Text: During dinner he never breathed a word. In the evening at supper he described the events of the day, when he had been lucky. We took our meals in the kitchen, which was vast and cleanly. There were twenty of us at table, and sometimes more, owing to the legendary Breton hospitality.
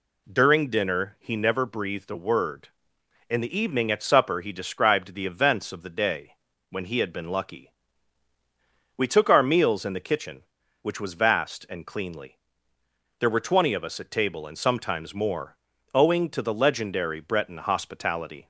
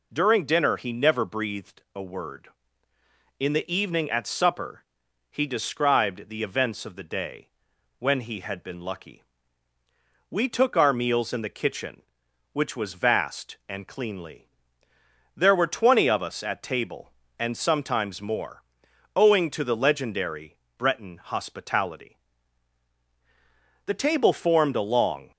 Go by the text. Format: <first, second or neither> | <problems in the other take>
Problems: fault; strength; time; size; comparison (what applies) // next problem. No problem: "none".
first | pauses between "supper" and "he"; noticeable; at 4.8 s; 0.46 s long // pauses between "legendary" and "Breton"; slight; at 20.5 s; 0.22 s long // goes on to say "The table formed a long"; from 23.8 s on; 1.4 s long